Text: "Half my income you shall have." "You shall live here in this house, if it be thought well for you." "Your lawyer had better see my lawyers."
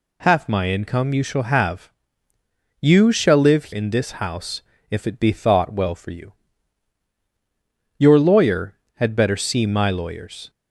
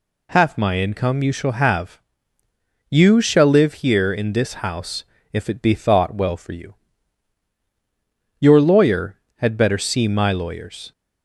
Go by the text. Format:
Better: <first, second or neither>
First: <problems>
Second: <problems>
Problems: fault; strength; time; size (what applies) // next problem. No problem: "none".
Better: second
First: skips "here"; at 3.7 s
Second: none